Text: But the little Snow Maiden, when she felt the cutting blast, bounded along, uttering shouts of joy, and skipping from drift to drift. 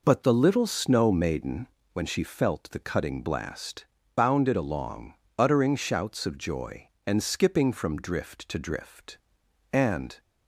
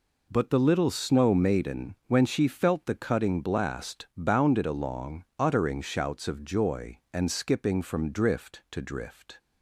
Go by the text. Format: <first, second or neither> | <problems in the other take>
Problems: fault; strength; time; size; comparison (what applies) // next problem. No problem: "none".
second | goes on to say "And"; slight; from 9.7 s on; 0.48 s long